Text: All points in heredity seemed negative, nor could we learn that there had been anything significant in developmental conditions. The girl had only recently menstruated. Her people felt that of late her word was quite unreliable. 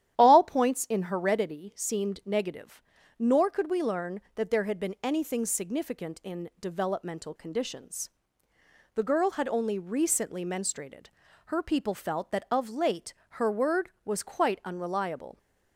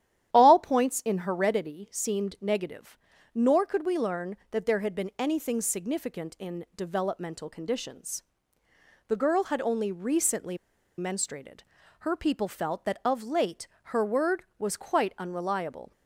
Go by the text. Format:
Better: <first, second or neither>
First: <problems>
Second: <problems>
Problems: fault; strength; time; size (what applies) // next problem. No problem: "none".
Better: first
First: starts louder than the rest; strong; until 1.1 s; 11 dB // pauses between "late" and "her"; slight; at 13.1 s; 0.18 s long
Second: starts louder than the rest; strong; until 1.3 s; 11 dB // pauses between "recently" and "menstruated"; at 10.5 s; 0.41 s long // pauses between "late" and "her"; slight; at 13.6 s; 0.18 s long